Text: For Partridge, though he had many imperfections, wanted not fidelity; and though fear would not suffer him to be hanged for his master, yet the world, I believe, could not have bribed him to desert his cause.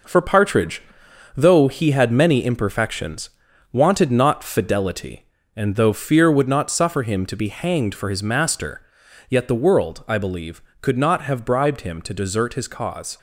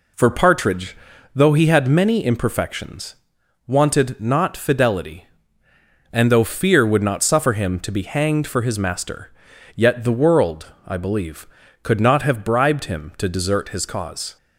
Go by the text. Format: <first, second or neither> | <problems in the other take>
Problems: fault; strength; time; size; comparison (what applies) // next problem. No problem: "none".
second | gets quieter; throughout; 6.5 dB